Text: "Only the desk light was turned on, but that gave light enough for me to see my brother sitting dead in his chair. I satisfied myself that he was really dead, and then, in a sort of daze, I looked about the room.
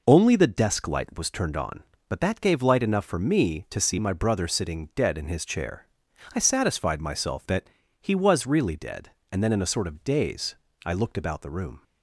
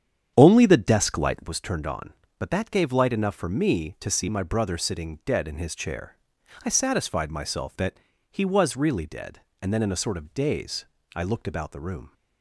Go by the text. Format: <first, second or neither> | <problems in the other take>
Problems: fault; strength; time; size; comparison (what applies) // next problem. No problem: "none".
first | starts louder than the rest; strong; until 1.5 s; 8.5 dB // pauses between "that" and "he"; slight; at 7.9 s; 0.34 s long; slight in the first